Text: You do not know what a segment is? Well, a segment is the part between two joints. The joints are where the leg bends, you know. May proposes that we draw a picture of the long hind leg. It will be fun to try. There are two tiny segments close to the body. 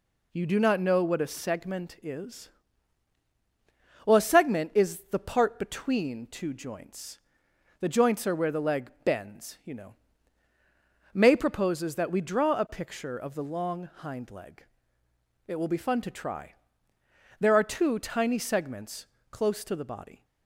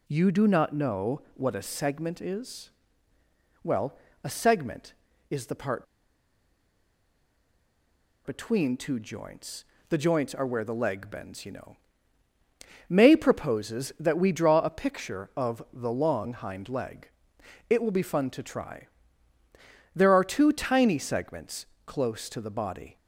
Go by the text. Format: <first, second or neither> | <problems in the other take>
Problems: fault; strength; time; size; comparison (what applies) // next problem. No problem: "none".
first | pauses between "part" and "between"; strong; at 5.8 s; 2.3 s long // pauses between "segments" and "close"; slight; at 21.6 s; 0.20 s long; slight in the first